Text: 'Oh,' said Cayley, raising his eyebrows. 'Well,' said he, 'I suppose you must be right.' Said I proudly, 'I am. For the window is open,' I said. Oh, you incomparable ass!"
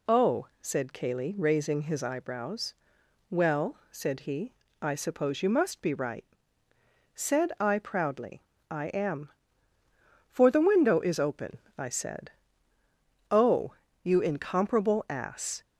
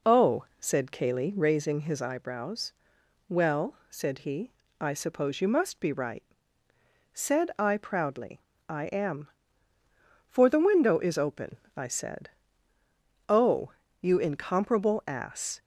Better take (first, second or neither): first